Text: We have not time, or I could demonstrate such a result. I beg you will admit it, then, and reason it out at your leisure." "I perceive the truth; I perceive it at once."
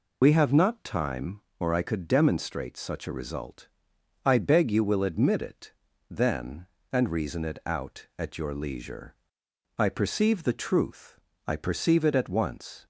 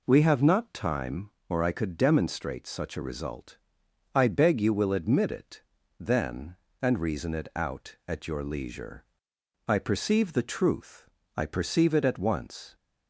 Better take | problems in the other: second | loses the start of "We"; at 0.2 s; 65 ms

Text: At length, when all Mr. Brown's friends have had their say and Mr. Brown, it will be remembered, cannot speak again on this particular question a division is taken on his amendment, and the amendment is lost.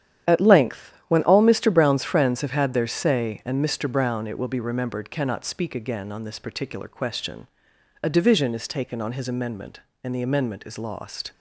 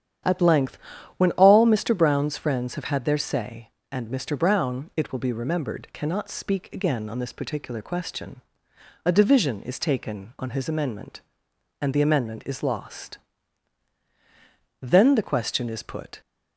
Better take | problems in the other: first | starts louder than the rest; strong; until 1.6 s; 9.5 dB; strong in the first // pauses between "question" and "a"; noticeable; at 8.4 s; 0.64 s long; noticeable in the first // goes on to say "Then the question is put"; from 14.8 s on; 1.4 s long

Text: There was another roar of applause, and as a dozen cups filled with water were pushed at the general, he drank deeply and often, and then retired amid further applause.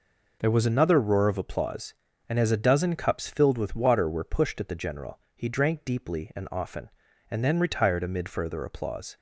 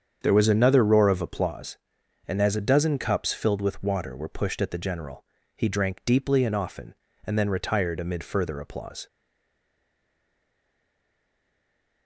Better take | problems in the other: first | starts louder than the rest; strong; until 1.2 s; 7.5 dB // stays silent after the last word; strong; from 9.0 s on; 3.0 s long

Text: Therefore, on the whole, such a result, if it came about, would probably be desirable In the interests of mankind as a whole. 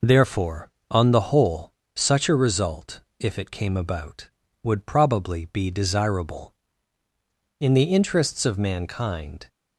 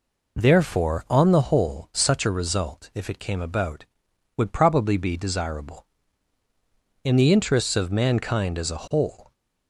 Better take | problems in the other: second | stops before "as a whole"; at 9.4 s

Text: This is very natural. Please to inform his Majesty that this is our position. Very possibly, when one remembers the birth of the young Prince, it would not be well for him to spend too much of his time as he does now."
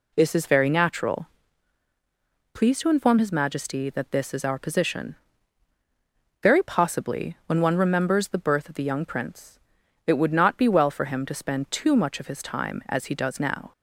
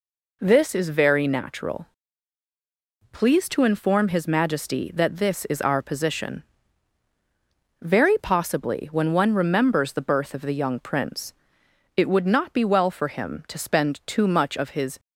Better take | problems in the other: first | stops before "time as he does now"; at 14.9 s

